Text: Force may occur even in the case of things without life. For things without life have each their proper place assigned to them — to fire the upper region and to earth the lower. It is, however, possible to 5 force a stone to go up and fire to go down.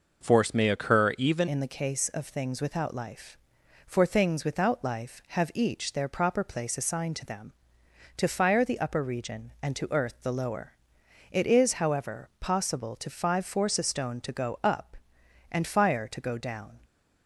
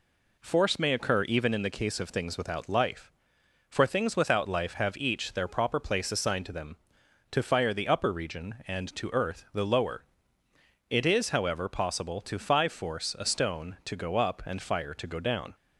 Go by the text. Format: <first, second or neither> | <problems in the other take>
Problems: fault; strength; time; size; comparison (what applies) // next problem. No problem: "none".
second | changes voice at "in"; from 1.4 s on; 15.4 s long